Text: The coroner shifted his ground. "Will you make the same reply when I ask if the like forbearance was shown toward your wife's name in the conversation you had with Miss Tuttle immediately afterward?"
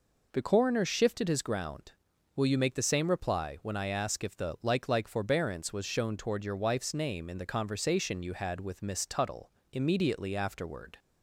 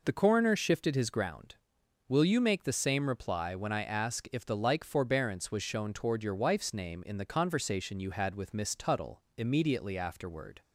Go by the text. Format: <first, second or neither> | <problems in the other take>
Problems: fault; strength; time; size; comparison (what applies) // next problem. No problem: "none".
second | says "like" twice; at 4.8 s // pauses between "Tuttle" and "immediately"; slight; at 9.5 s; 0.22 s long; slight in the second